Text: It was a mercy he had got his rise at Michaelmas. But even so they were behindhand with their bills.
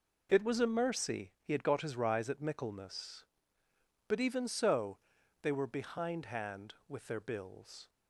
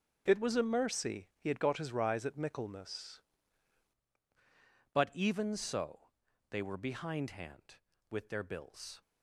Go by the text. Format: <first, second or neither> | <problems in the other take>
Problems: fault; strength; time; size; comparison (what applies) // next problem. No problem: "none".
first | starts louder than the rest; strong; until 1.2 s; 7 dB // changes voice at "But"; from 4.9 s on; 4.1 s long // pauses between "so" and "they"; at 6.0 s; 0.40 s long; also in the first